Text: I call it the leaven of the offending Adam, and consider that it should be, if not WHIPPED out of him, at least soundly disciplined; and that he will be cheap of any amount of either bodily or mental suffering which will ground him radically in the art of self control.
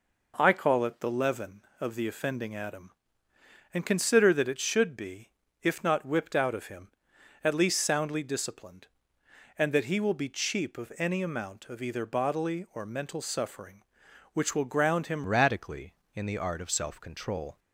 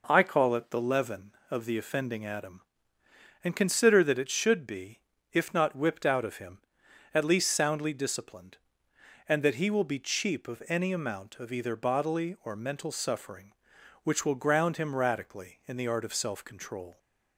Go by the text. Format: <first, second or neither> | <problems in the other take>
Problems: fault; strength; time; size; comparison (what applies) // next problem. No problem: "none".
second | changes voice at "radically"; from 15.2 s on; 2.3 s long